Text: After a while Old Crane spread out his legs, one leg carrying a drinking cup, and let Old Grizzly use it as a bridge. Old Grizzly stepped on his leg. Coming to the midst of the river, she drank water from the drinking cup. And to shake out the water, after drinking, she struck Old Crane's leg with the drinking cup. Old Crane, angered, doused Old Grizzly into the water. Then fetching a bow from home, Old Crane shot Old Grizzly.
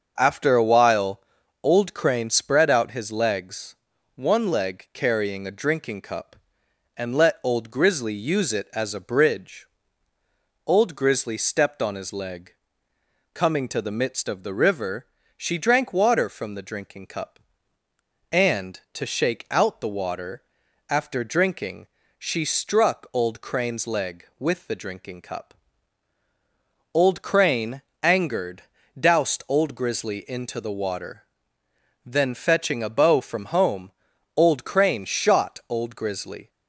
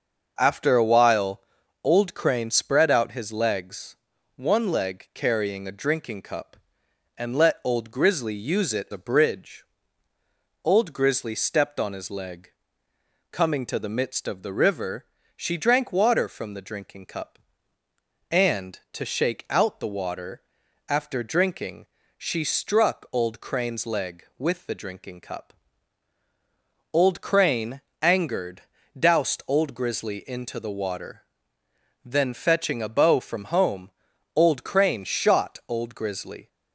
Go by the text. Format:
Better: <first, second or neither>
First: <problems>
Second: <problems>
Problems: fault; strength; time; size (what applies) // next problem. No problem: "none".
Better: first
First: starts louder than the rest; until 1.1 s; 6.5 dB // pauses between "while" and "Old"; at 1.2 s; 0.40 s long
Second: starts louder than the rest; until 1.3 s; 6 dB // pauses between "while" and "Old"; at 1.4 s; 0.40 s long // skips "as"; at 8.8 s